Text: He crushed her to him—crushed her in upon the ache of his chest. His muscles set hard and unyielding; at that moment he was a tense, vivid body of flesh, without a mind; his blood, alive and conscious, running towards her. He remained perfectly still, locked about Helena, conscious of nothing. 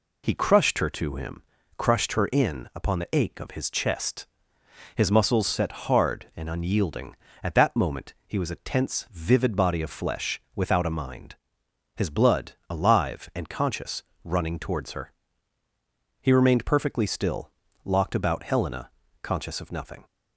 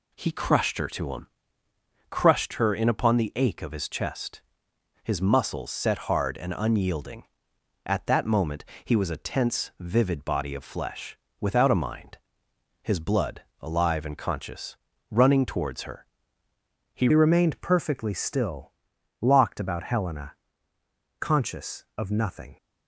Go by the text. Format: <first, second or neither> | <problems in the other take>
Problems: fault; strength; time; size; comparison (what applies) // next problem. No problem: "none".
first | pauses between "moment" and "he"; slight; at 8.6 s; 0.22 s long // changes voice at "remained"; from 17.1 s on; 5.4 s long